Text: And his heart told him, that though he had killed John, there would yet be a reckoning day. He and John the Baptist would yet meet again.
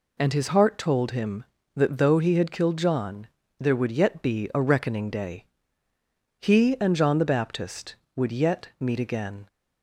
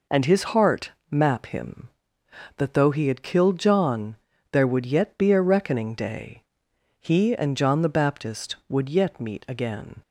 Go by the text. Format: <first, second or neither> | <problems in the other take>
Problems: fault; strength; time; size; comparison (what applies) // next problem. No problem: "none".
first | says "map" for "told"; at 1.0 s